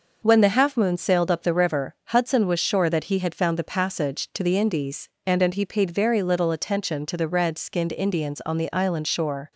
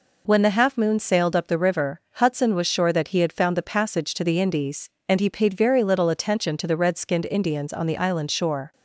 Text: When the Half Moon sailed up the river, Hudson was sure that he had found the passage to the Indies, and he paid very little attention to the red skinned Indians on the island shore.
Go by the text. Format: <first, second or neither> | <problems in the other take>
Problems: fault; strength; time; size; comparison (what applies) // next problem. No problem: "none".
second | says "and" twice; at 5.4 s